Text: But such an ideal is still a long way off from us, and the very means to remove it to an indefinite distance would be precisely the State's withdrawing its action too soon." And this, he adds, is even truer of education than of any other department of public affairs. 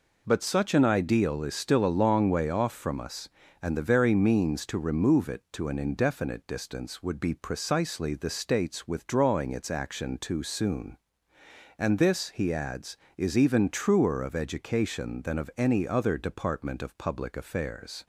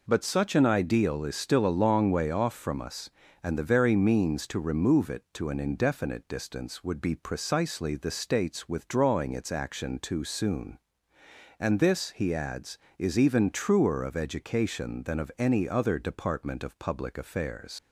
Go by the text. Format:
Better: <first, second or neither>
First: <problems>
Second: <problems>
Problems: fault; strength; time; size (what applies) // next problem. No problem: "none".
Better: first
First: none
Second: leaves "affairs" unfinished; at 17.7 s; 80 ms